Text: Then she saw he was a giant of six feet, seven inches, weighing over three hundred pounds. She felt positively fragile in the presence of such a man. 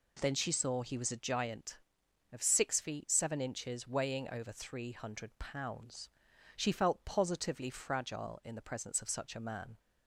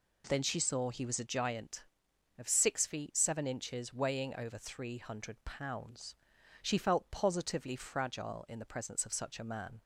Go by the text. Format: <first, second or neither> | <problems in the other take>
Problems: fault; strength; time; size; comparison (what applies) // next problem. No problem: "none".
neither | none